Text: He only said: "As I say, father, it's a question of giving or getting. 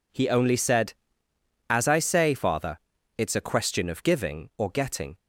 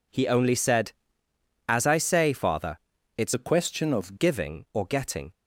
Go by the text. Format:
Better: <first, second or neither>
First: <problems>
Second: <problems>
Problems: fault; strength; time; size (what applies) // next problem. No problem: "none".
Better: first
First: none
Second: changes voice from "a" to "of"; from 3.3 to 4.1 s; 0.8 s long